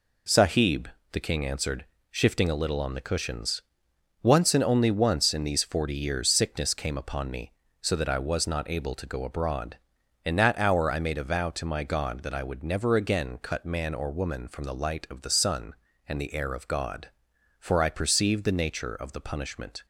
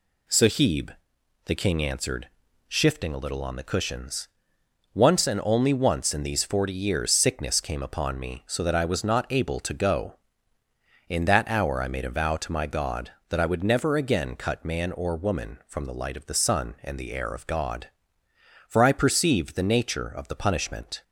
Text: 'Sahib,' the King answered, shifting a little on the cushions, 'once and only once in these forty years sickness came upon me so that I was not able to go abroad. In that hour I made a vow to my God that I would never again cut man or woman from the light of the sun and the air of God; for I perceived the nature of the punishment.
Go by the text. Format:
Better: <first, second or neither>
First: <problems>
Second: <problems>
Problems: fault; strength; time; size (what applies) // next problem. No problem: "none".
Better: first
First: none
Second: skips "abroad"; at 10.6 s